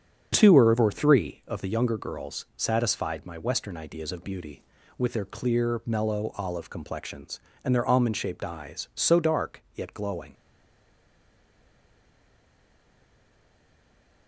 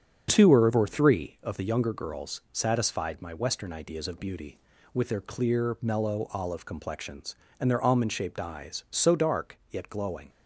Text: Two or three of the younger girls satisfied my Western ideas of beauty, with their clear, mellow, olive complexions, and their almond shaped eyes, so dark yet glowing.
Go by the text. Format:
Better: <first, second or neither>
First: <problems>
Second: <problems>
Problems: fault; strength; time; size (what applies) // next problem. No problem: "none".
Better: second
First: starts louder than the rest; strong; until 1.3 s; 7.5 dB // stays silent after the last word; strong; from 10.3 s on; 3.9 s long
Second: starts louder than the rest; strong; until 1.3 s; 7.5 dB